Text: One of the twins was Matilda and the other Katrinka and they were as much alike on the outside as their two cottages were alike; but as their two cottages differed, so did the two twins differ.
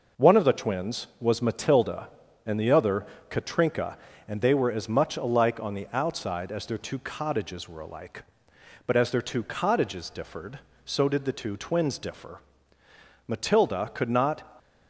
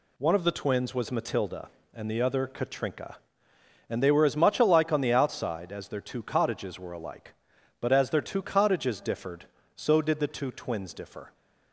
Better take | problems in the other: second | pauses between "other" and "Katrinka"; slight; at 3.0 s; 0.22 s long // goes on to say "Matilda could not"; noticeable; from 13.2 s on; 1.1 s long

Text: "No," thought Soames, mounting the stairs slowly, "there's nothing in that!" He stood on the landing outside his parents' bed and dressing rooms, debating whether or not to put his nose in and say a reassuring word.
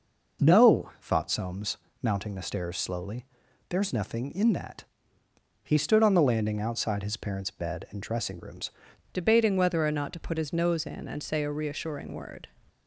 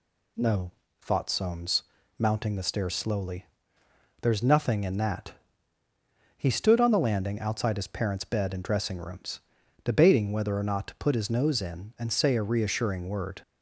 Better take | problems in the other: second | changes voice at "debating"; from 9.1 s on; 3.3 s long

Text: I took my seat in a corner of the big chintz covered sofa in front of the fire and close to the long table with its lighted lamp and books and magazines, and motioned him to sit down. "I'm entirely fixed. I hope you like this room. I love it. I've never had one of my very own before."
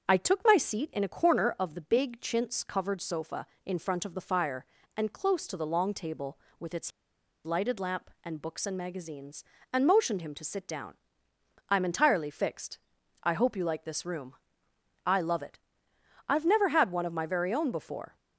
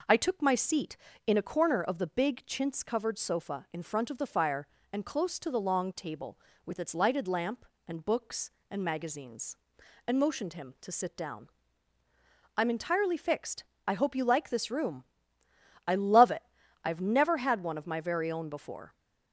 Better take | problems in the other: second | starts louder than the rest; until 1.1 s; 7 dB // pauses between "its" and "lighted"; noticeable; at 6.9 s; 0.54 s long

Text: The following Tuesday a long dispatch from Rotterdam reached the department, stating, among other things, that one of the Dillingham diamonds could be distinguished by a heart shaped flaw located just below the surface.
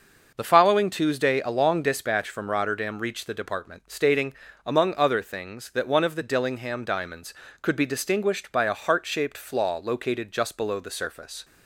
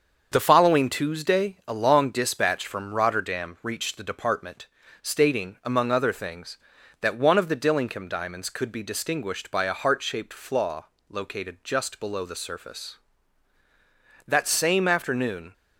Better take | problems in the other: first | starts louder than the rest; until 1.3 s; 7 dB // pauses between "flaw" and "located"; slight; at 10.8 s; 0.24 s long // goes on to say "That same afternoon"; noticeable; from 14.2 s on; 1.2 s long

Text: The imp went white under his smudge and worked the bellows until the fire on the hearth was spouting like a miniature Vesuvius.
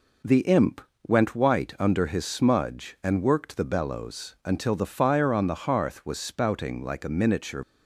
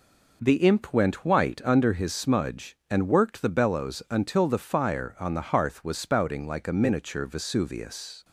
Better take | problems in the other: second | pauses between "imp" and "went"; slight; at 0.8 s; 0.26 s long // stops before "Vesuvius"; at 7.6 s

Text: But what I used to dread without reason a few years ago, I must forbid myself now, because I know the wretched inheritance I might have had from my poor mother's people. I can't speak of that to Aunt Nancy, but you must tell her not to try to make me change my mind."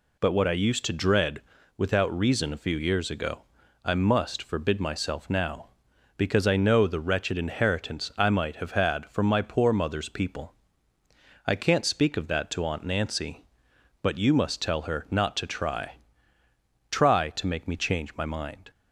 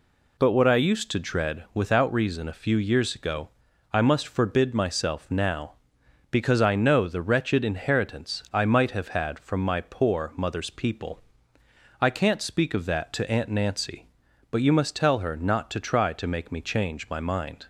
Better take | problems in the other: second | pauses between "dread" and "without"; slight; at 1.4 s; 0.34 s long // says "try" twice; at 16.9 s

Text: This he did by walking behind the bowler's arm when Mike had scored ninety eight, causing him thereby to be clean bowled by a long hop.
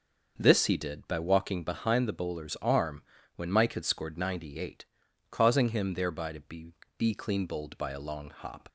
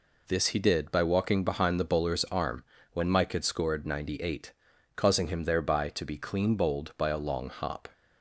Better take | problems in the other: second | starts louder than the rest; noticeable; until 1.3 s; 6 dB // pauses between "arm" and "when"; slight; at 3.0 s; 0.34 s long; slight in the second // says "be" twice; at 6.9 s

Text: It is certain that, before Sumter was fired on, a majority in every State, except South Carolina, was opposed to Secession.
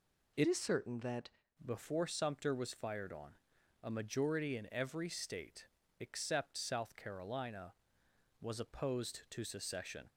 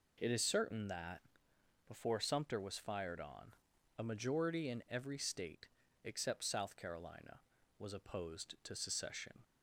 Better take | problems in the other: second | changes voice from "is" to "that"; from 0.4 to 1.2 s; 0.8 s long

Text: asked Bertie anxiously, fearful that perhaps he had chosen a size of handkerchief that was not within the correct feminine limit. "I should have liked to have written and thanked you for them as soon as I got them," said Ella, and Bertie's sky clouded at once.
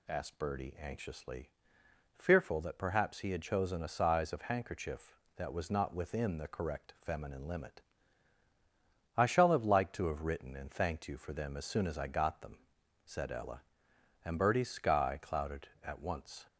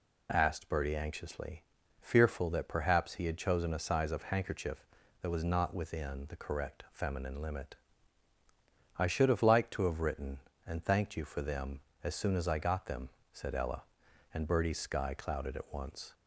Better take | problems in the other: second | says "shall" for "should"; at 9.2 s

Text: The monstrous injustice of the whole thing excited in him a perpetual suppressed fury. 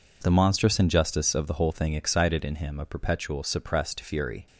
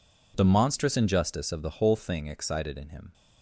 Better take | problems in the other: first | stops before "a perpetual suppressed fury"; at 3.1 s

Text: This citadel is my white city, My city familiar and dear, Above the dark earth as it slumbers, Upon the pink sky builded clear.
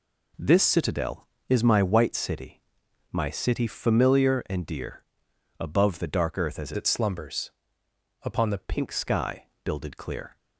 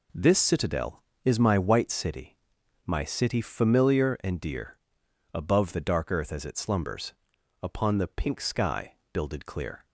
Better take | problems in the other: second | changes voice from "it" to "the"; from 6.7 to 8.5 s; 1.8 s long // pauses between "sky" and "builded"; slight; at 9.4 s; 0.18 s long; slight in the second

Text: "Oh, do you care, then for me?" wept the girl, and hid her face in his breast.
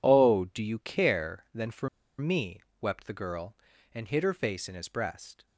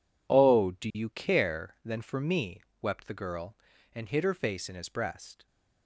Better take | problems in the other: second | pauses between "for" and "me"; slight; at 1.8 s; 0.31 s long

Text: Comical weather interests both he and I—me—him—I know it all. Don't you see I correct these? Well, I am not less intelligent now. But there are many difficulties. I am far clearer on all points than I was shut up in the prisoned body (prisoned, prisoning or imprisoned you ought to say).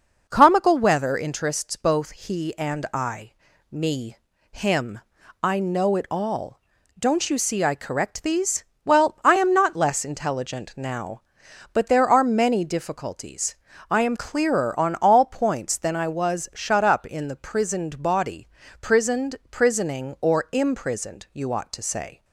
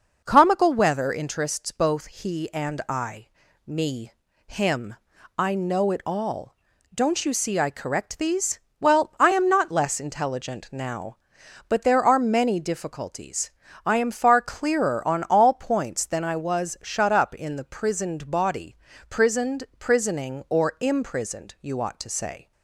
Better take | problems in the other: second | skips "far"; at 14.1 s

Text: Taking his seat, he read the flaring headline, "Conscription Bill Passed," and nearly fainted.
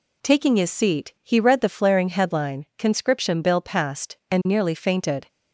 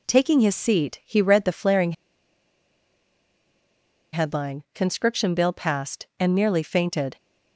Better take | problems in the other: first | pauses between "flaring" and "headline"; strong; at 1.9 s; 2.2 s long

